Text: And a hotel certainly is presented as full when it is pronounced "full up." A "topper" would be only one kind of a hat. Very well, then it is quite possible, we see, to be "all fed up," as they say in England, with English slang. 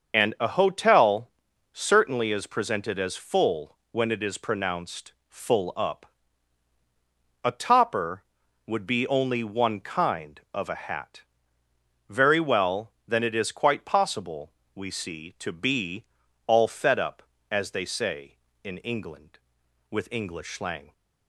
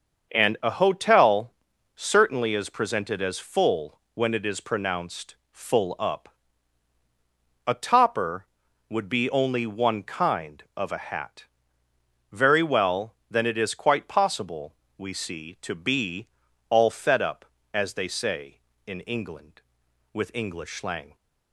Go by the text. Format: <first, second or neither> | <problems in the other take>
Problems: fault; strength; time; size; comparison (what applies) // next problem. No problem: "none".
second | loses the start of "And"; at 0.1 s; 65 ms // starts louder than the rest; until 1.1 s; 6.5 dB; also in the second // pauses between "hotel" and "certainly"; at 1.3 s; 0.42 s long; also in the second // pauses between "full" and "when"; slight; at 3.7 s; 0.16 s long; slight in the second // pauses between "pronounced" and "full"; slight; at 5.1 s; 0.16 s long; slight in the second // pauses between "be" and "all"; at 16.0 s; 0.42 s long; also in the second